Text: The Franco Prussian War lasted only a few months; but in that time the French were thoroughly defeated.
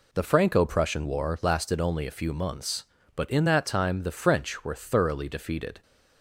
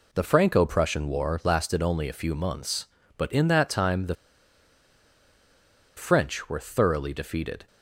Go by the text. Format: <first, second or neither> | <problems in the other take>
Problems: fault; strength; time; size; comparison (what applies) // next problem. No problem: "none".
first | pauses between "the" and "French"; strong; at 4.1 s; 1.8 s long